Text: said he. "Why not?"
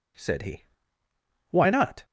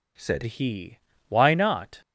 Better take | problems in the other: first | changes voice at "he"; from 0.4 s on; 1.5 s long

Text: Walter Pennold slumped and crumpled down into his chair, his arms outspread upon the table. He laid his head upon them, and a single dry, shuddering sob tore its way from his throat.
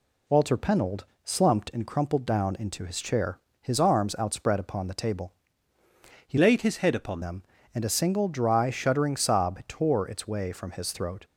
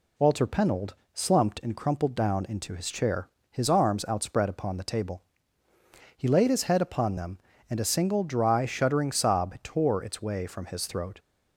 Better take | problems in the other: second | pauses between "Pennold" and "slumped"; slight; at 1.0 s; 0.18 s long; slight in the second // changes voice from "laid" to "upon"; from 6.3 to 7.2 s; 0.9 s long

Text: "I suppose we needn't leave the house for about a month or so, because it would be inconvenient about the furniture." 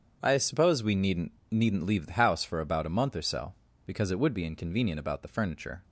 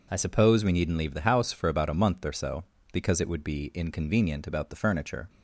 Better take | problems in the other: second | starts louder than the rest; strong; until 1.2 s; 7.5 dB // says "needn't" twice; at 1.4 s

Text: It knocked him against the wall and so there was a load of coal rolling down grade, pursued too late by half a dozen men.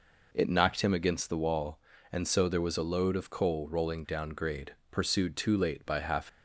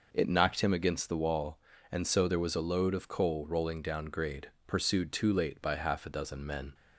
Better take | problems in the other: second | stops before "a dozen men"; at 6.2 s

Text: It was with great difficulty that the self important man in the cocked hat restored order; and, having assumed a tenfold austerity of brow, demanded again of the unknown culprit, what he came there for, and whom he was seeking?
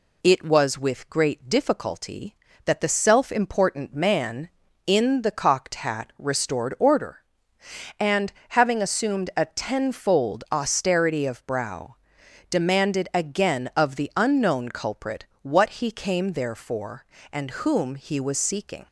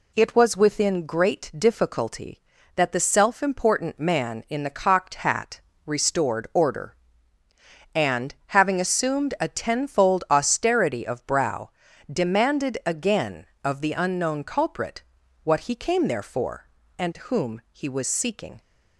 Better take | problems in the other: first | says "within" for "with"; at 0.5 s // pauses between "hat" and "restored"; slight; at 5.6 s; 0.26 s long

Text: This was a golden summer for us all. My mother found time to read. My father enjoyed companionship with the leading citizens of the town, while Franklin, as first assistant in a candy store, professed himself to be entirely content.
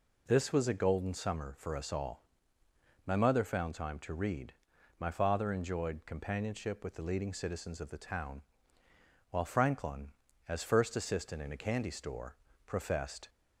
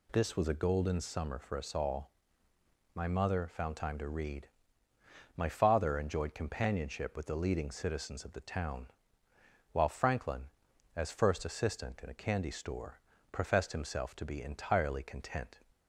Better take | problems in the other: second | stops before "himself to be entirely content"; at 13.2 s

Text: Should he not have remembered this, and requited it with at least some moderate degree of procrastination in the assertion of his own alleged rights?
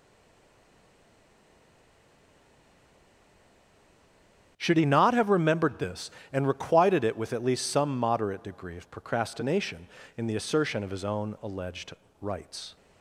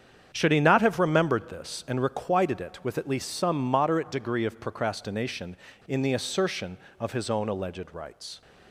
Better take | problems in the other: second | stays silent before the first word; strong; until 4.5 s; 4.5 s long // starts louder than the rest; strong; until 5.5 s; 8.5 dB; strong in the second // pauses between "alleged" and "rights"; slight; at 11.9 s; 0.30 s long

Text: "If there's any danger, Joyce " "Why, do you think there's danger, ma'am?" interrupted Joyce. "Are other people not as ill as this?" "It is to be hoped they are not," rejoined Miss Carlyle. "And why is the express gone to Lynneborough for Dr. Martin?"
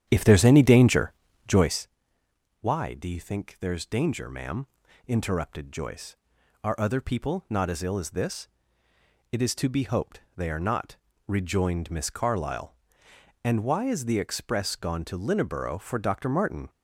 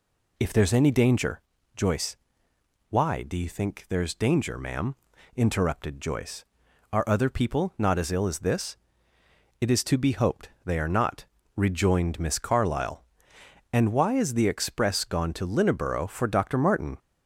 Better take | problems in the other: second | starts louder than the rest; strong; until 1.9 s; 10 dB

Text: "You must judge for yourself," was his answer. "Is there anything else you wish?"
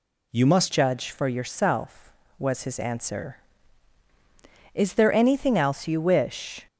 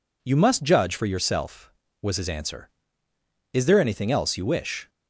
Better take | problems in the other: second | changes voice at "judge"; from 0.7 s on; 5.9 s long

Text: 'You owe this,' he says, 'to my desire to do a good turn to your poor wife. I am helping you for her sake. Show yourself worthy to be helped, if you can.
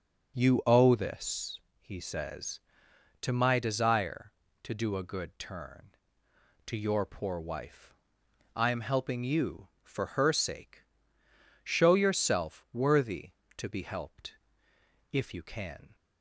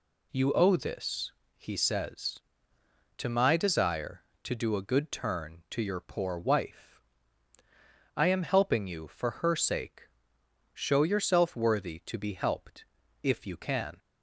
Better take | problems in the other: neither | none

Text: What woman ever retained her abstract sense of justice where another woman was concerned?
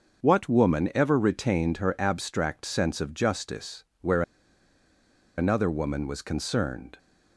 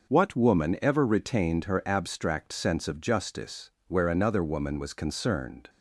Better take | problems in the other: second | starts louder than the rest; until 1.2 s; 6.5 dB; also in the second // pauses between "justice" and "where"; slight; at 3.8 s; 0.16 s long; slight in the second // pauses between "where" and "another"; at 4.2 s; 1.1 s long

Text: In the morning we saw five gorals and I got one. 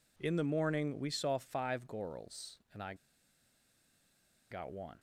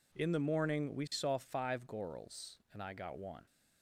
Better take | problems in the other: second | pauses between "I" and "got"; strong; at 2.9 s; 1.5 s long

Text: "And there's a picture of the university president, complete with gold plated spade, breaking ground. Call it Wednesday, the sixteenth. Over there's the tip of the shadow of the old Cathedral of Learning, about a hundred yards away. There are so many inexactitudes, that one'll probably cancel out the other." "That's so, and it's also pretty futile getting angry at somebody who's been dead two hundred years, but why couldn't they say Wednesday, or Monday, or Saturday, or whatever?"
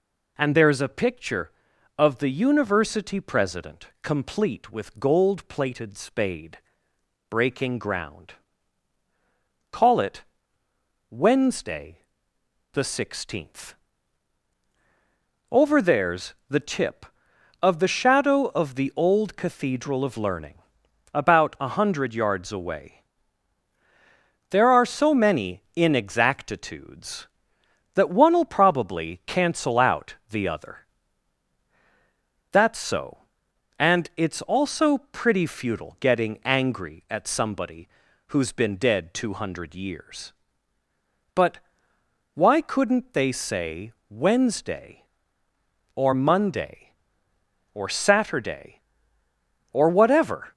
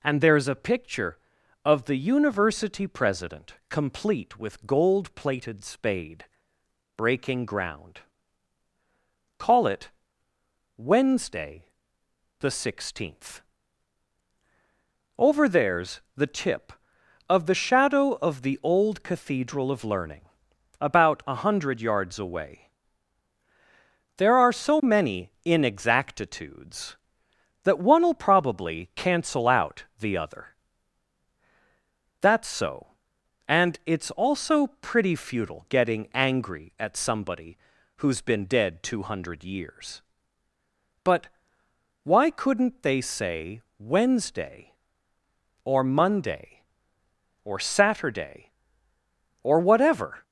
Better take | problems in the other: neither | pauses between "it" and "Wednesday"; noticeable; the same in both // pauses between "somebody" and "who's"; the same in both // pauses between "but" and "why"; noticeable; the same in both // pauses between "say" and "Wednesday"; slight; the same in both

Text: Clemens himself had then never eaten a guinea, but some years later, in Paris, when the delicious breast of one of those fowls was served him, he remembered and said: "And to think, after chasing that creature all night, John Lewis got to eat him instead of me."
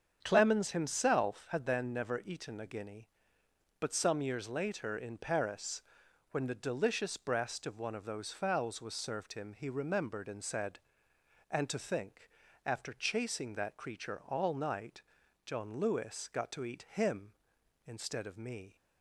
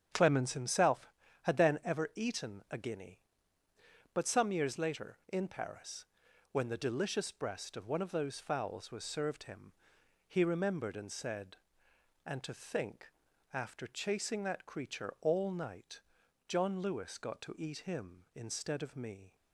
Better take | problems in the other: first | starts louder than the rest; strong; until 1.4 s; 8 dB; strong in the first // says "ever" for "never"; at 1.8 s

